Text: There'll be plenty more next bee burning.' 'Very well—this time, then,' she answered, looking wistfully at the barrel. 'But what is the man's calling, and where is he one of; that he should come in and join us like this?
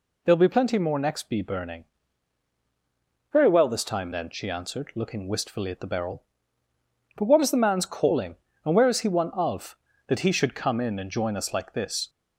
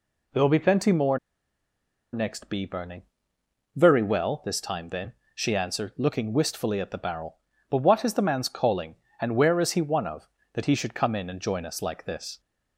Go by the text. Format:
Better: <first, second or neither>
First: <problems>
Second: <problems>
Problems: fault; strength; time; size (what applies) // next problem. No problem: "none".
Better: first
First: none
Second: pauses between "more" and "next"; noticeable; at 1.1 s; 0.95 s long